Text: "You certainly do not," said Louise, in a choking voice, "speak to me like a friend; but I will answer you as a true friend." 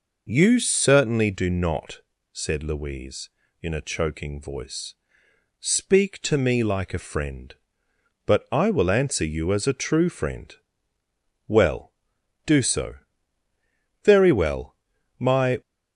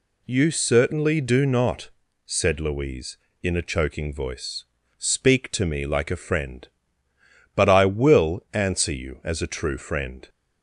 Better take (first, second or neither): second